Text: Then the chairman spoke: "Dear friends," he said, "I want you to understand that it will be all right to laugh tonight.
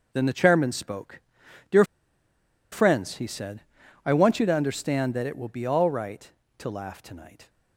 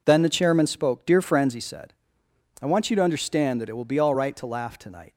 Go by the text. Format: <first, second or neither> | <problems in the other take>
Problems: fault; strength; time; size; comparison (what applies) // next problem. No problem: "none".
second | pauses between "Dear" and "friends"; noticeable; at 1.8 s; 0.88 s long